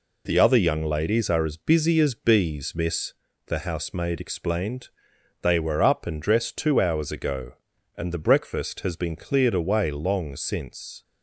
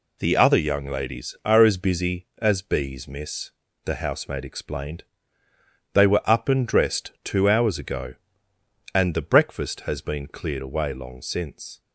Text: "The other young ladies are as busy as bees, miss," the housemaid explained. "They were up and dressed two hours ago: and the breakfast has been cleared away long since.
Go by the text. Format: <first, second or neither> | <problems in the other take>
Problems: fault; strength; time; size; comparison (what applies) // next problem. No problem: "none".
neither | none